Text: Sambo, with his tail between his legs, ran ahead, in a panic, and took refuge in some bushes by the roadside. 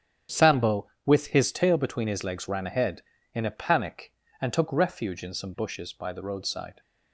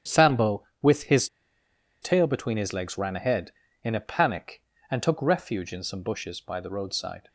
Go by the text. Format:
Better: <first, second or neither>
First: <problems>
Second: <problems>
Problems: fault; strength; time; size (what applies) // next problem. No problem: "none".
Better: first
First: starts louder than the rest; strong; until 1.4 s; 9 dB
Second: starts louder than the rest; strong; until 1.2 s; 9 dB // pauses between "his" and "tail"; noticeable; at 1.2 s; 0.75 s long